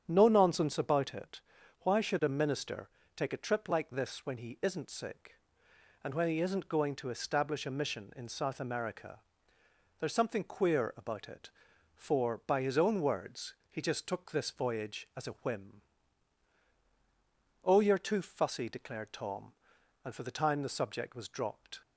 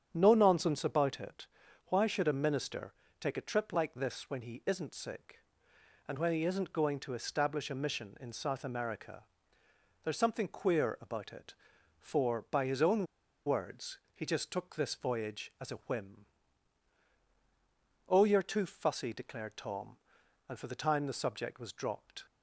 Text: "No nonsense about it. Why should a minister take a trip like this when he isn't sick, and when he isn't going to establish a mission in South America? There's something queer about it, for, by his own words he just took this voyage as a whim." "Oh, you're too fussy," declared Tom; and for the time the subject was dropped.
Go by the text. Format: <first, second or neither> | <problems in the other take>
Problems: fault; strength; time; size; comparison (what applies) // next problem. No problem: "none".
first | starts louder than the rest; strong; until 1.1 s; 8.5 dB; strong in the first // pauses between "minister" and "take"; slight; at 2.9 s; 0.28 s long; slight in the first // pauses between "own" and "words"; at 13.0 s; 0.40 s long // pauses between "words" and "he"; slight; at 13.9 s; 0.16 s long; slight in the first